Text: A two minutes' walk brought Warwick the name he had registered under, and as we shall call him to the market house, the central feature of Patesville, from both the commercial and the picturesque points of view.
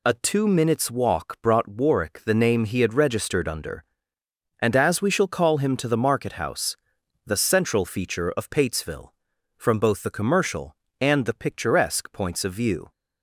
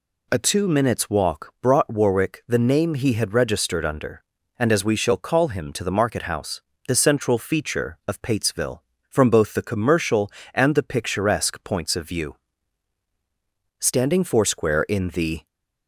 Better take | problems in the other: first | goes on to say "Standing foursquare in the"; strong; from 13.7 s on; 1.6 s long

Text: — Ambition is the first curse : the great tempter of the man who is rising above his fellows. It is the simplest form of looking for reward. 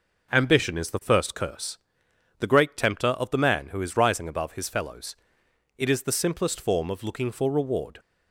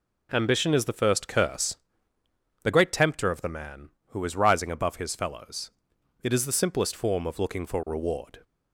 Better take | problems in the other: neither | none

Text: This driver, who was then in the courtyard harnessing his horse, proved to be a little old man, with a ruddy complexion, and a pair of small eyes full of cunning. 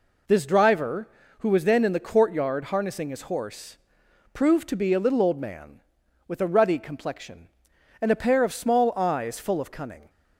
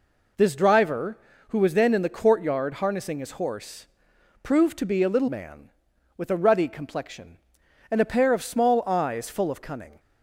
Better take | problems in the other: first | skips "old"; at 5.2 s

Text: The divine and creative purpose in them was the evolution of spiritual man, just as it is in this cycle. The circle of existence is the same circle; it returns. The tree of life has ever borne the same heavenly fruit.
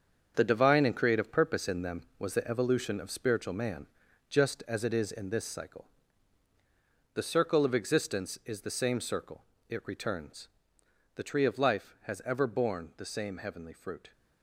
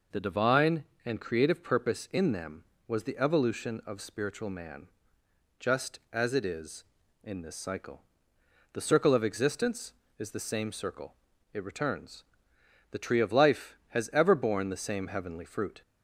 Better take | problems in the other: second | gets quieter; strong; throughout; 9.5 dB

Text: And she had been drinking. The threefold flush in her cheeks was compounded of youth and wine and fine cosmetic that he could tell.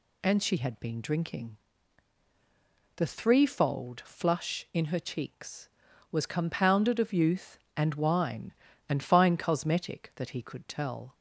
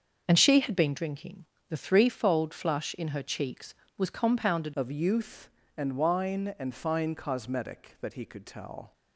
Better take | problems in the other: first | starts louder than the rest; until 1.2 s; 6.5 dB // changes voice at "of"; from 4.7 s on; 4.2 s long

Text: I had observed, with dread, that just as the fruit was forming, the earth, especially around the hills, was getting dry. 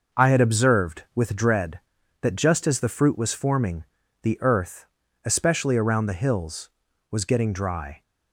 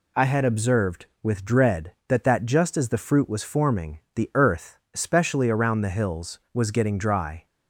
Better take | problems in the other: first | says "that" twice; at 2.2 s

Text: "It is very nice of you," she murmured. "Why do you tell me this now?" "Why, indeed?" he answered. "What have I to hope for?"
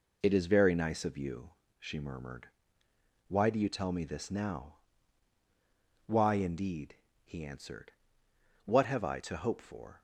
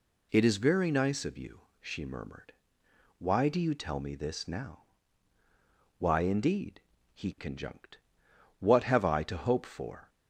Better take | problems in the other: first | says "conjunct" for "answered"; at 7.3 s

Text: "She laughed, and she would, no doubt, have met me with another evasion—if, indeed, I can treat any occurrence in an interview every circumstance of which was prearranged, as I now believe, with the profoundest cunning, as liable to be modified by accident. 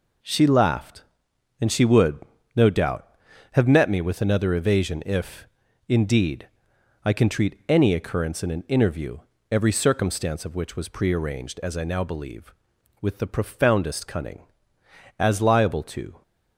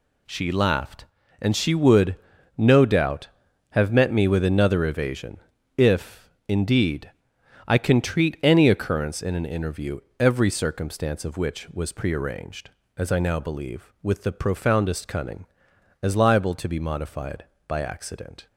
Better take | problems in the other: second | pauses between "interview" and "every"; slight; at 9.1 s; 0.32 s long; slight in the second // stops before "be modified by accident"; at 16.2 s

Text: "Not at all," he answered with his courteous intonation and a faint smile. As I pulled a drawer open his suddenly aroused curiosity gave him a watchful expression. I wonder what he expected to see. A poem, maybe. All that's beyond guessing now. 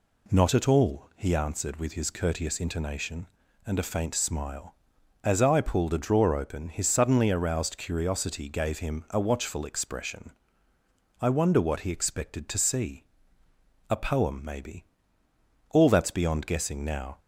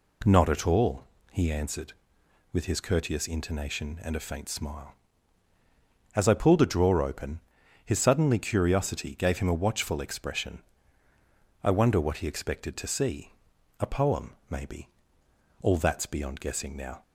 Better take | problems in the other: first | pauses between "open" and "his"; at 7.4 s; 0.44 s long // skips "aroused"; at 8.3 s

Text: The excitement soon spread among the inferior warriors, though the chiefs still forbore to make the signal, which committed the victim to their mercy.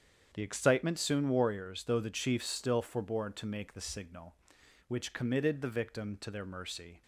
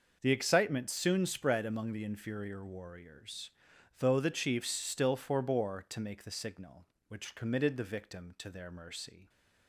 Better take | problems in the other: second | starts louder than the rest; strong; until 1.3 s; 8 dB // skips "spread among the inferior"; at 1.2 s

